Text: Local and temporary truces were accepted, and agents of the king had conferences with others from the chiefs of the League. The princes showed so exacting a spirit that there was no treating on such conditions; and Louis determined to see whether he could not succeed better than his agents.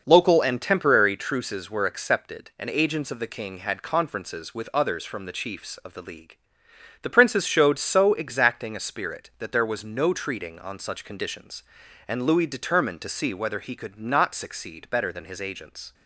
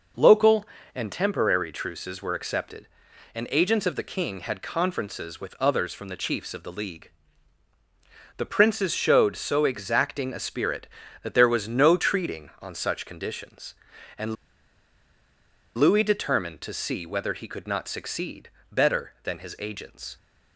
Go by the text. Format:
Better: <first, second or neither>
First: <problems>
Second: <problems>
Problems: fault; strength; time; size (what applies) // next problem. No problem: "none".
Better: first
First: none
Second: pauses between "and" and "Louis"; strong; at 14.3 s; 1.4 s long // pauses between "succeed" and "better"; slight; at 18.4 s; 0.24 s long